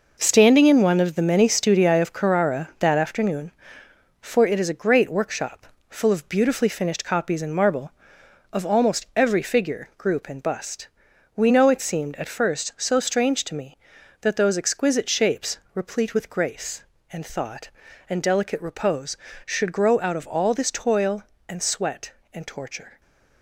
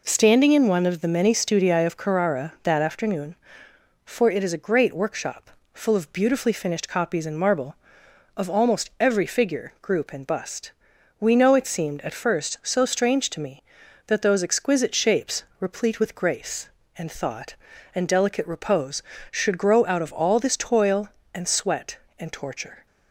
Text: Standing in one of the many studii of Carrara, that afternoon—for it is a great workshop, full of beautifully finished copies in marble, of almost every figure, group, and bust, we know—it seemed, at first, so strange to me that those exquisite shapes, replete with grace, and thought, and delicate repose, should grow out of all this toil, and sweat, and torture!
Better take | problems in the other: second | gets quieter; strong; throughout; 9 dB

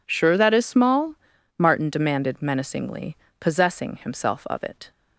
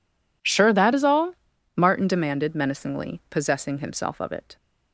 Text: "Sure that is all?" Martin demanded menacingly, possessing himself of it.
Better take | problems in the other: second | says "small" for "all"; at 0.6 s

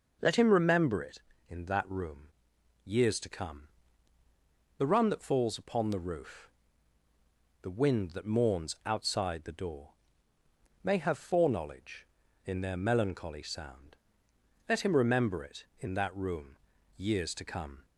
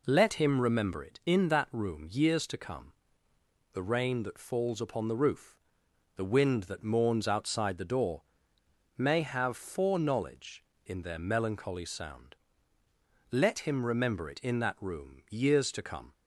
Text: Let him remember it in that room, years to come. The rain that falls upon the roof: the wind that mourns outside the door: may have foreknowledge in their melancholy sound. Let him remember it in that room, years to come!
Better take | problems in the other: second | says "run" for "rain"; at 4.8 s

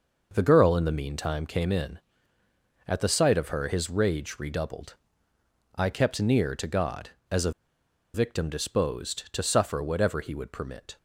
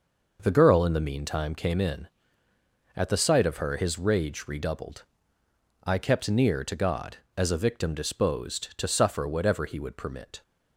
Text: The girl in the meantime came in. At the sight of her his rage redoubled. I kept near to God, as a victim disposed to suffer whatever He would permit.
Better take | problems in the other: second | pauses between "a" and "victim"; noticeable; at 7.5 s; 0.62 s long

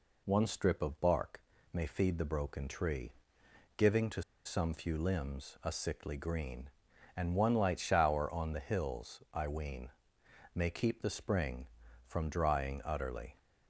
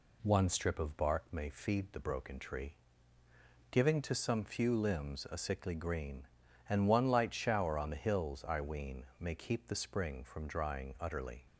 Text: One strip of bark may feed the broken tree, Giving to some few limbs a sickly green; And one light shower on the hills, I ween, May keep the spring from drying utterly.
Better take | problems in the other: second | pauses between "bark" and "may"; slight; at 1.3 s; 0.34 s long // pauses between "to" and "some"; slight; at 4.2 s; 0.23 s long

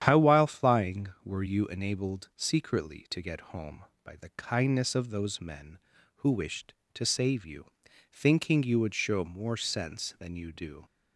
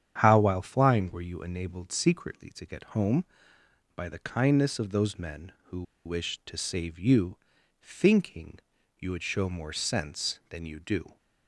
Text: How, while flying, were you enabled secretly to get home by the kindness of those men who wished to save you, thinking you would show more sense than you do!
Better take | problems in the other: first | starts louder than the rest; strong; until 1.2 s; 9 dB; strong in the first // pauses between "who" and "wished"; slight; at 5.8 s; 0.23 s long // pauses between "thinking" and "you"; at 8.5 s; 0.40 s long

